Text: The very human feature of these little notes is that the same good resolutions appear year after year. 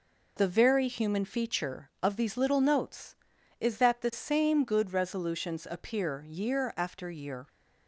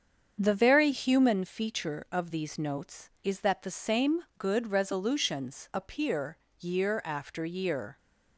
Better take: first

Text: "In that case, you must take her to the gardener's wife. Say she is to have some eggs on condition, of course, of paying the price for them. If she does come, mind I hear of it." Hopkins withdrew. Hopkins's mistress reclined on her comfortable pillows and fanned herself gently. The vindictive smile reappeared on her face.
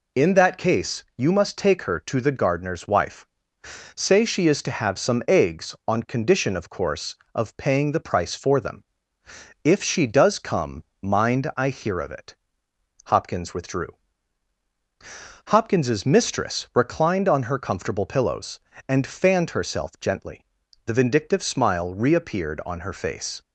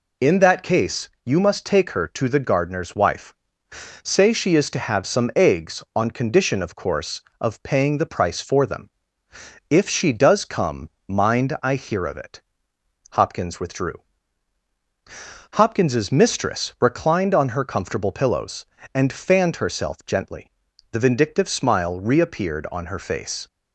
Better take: neither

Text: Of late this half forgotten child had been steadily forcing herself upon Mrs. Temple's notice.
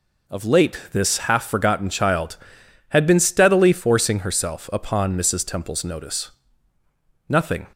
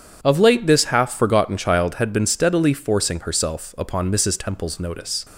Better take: second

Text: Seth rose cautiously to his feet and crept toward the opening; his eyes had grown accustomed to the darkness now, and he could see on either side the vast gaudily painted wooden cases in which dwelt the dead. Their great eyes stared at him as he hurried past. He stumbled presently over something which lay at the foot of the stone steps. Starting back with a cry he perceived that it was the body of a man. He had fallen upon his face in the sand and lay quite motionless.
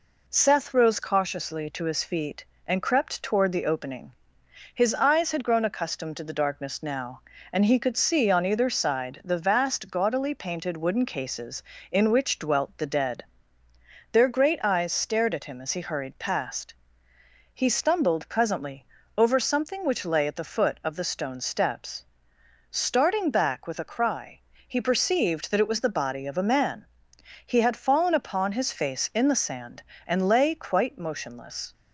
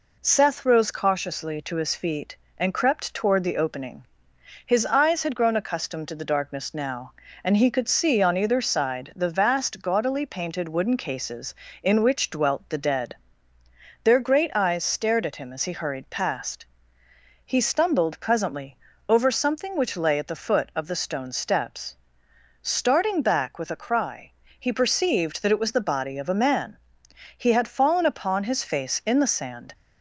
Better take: first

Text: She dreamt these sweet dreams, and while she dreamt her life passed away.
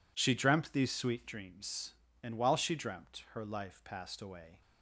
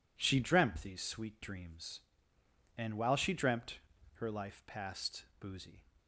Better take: first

